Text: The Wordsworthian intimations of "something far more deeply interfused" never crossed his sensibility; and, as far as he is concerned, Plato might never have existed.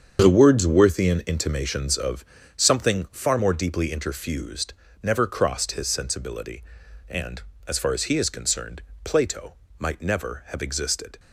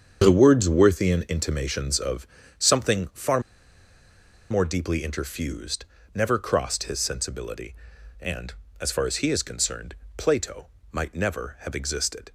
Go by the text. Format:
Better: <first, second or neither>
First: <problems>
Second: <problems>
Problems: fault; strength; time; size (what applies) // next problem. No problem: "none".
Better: first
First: starts louder than the rest; strong; until 1.2 s; 7.5 dB // pauses between "of" and "something"; slight; at 2.2 s; 0.28 s long // pauses between "interfused" and "never"; slight; at 4.7 s; 0.28 s long // pauses between "Plato" and "might"; slight; at 9.5 s; 0.24 s long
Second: starts louder than the rest; strong; until 1.2 s; 7.5 dB // pauses between "of" and "something"; slight; at 2.2 s; 0.28 s long // pauses between "far" and "more"; at 3.4 s; 1.1 s long // pauses between "interfused" and "never"; slight; at 5.8 s; 0.28 s long // pauses between "Plato" and "might"; slight; at 10.6 s; 0.24 s long